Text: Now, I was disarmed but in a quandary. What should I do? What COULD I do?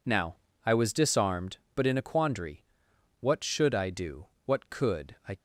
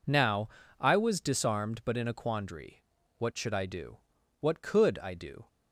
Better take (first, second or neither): second